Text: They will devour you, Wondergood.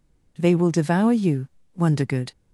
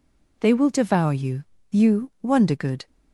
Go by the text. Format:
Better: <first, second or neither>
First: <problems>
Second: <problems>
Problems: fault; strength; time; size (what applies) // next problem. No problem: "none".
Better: first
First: none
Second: says "you" twice; at 1.7 s